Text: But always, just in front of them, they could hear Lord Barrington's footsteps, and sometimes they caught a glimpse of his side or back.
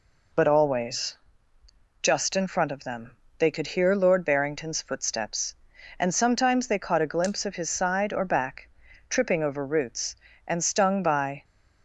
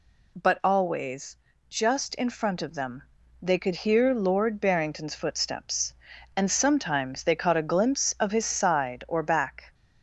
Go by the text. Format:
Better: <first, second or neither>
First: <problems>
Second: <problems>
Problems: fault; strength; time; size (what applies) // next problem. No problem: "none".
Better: second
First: goes on to say "Tripping over roots and stung by"; strong; from 9.0 s on; 2.3 s long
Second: none